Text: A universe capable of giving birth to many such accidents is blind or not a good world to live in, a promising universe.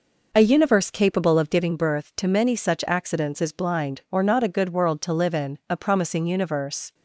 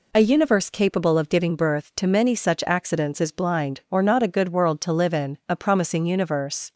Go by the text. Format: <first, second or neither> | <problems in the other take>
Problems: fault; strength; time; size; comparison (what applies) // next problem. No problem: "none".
second | starts louder than the rest; noticeable; until 1.6 s; 5 dB